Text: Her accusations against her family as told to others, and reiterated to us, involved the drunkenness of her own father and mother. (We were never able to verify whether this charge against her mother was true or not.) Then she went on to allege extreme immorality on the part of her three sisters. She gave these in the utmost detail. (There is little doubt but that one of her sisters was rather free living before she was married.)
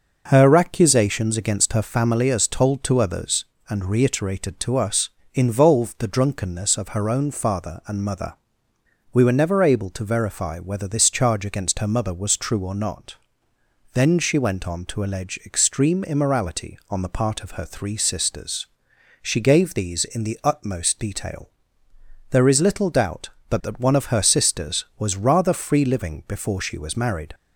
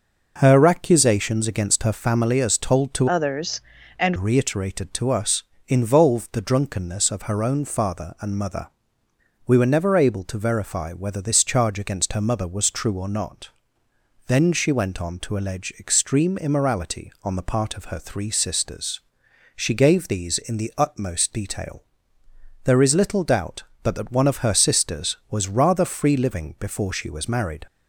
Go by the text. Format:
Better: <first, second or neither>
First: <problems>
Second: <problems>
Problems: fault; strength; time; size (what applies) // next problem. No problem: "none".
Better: first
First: none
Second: changes voice from "others" to "and"; from 3.0 to 4.1 s; 1.1 s long